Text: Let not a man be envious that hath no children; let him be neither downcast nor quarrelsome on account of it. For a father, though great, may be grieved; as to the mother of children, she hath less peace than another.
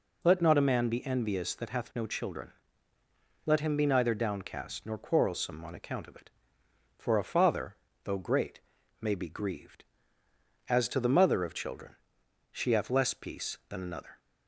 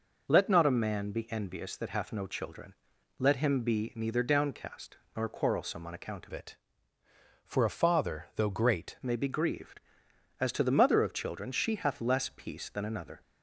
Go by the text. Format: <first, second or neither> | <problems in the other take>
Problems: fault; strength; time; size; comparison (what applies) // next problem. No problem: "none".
first | pauses between "downcast" and "nor"; slight; at 4.9 s; 0.20 s long // changes voice from "it" to "great"; from 6.3 to 8.9 s; 2.6 s long